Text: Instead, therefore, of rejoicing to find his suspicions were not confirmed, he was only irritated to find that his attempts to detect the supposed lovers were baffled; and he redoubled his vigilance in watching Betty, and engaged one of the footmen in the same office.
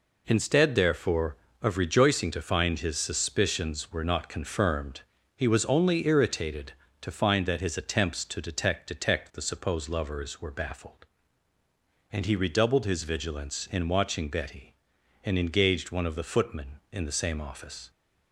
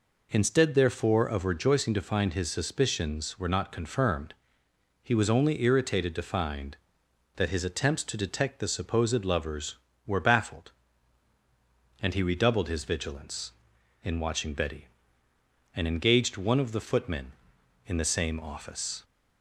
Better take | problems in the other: second | says "detect" twice; at 8.8 s

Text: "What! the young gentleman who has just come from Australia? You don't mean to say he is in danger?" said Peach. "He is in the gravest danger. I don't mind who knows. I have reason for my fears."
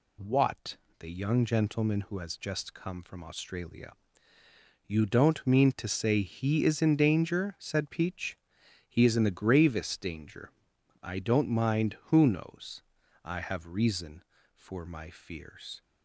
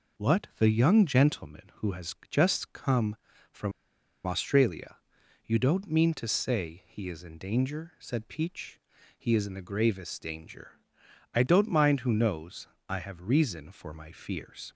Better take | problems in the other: first | pauses between "from" and "Australia"; noticeable; at 3.7 s; 0.53 s long

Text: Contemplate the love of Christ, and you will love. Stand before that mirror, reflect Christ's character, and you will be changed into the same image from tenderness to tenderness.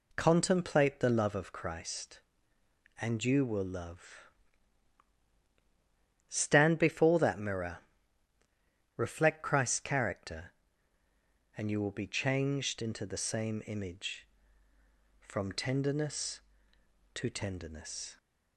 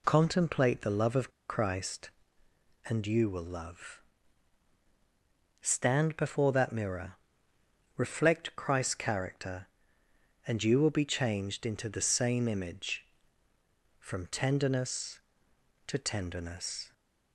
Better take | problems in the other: first | pauses between "of" and "Christ"; slight; at 1.3 s; 0.18 s long

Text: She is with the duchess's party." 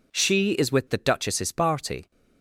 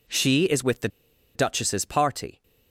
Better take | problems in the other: first | pauses between "the" and "duchess's"; noticeable; at 0.8 s; 0.47 s long

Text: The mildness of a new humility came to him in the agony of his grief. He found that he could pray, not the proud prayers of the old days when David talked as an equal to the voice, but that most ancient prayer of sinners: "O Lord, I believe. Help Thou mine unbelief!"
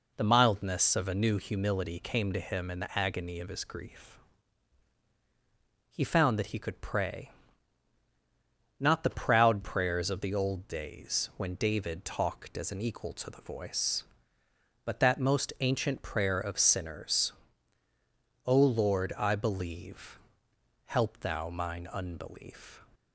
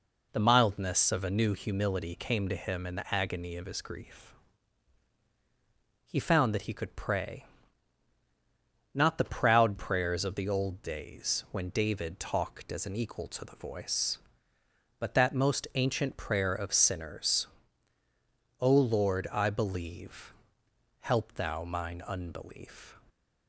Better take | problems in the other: neither | none

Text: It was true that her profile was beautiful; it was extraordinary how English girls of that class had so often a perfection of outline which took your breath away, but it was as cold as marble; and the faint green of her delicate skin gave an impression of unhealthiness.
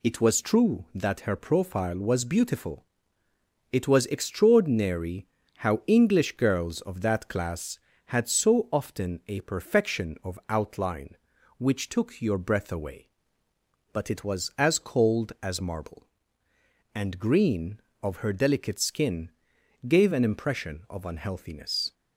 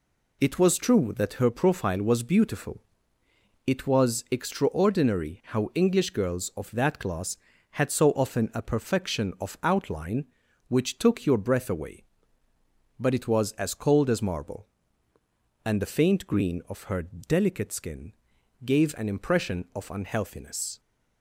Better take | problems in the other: second | pauses between "extraordinary" and "how"; slight; at 5.2 s; 0.30 s long // skips "the faint"; at 17.1 s // pauses between "skin" and "gave"; noticeable; at 19.3 s; 0.58 s long; noticeable in the second

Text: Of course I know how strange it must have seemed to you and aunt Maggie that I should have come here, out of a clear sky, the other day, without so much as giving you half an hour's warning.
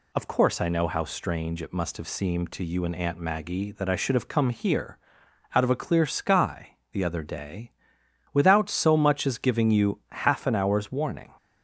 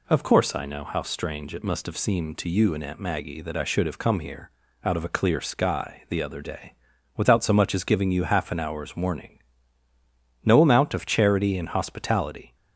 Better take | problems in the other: first | goes on to say "No amount of charity and hospitality"; strong; from 10.4 s on; 2.1 s long

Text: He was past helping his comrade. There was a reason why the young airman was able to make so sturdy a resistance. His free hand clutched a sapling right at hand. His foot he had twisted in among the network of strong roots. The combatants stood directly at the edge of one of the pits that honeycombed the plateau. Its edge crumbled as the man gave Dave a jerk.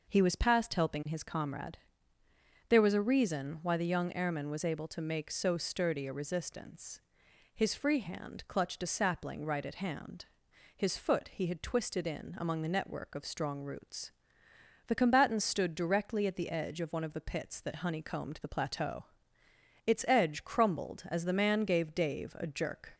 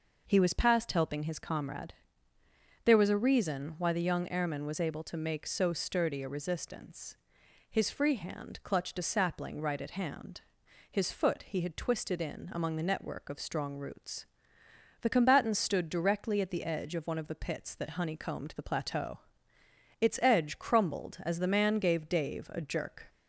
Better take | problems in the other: neither | none

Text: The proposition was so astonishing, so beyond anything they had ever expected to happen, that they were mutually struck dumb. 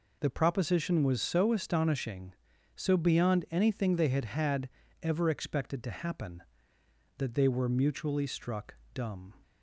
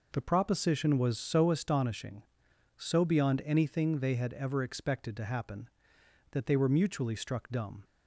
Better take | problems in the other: second | says "had" twice; at 4.2 s // pauses between "struck" and "dumb"; slight; at 8.7 s; 0.18 s long

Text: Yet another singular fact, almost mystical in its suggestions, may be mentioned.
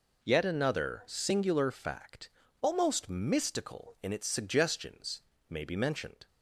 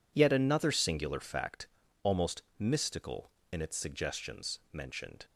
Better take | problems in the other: first | skips "may be"; at 4.6 s

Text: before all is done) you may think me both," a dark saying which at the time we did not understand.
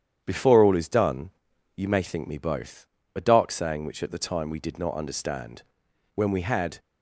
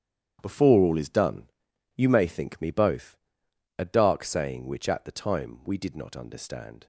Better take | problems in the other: second | starts louder than the rest; strong; until 1.2 s; 9 dB; strong in the second // goes on to say "When we had"; noticeable; from 6.1 s on; 0.64 s long

